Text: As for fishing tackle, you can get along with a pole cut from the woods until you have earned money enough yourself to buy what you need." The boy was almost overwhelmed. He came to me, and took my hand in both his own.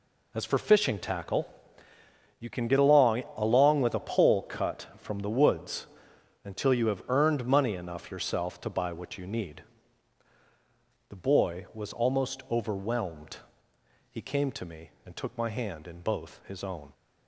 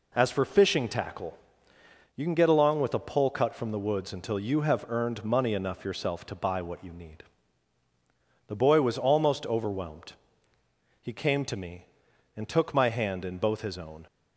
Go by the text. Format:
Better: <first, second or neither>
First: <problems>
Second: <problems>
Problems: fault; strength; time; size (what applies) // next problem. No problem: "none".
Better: second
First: says "along" twice; at 3.3 s // pauses between "woods" and "until"; noticeable; at 5.8 s; 0.58 s long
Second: none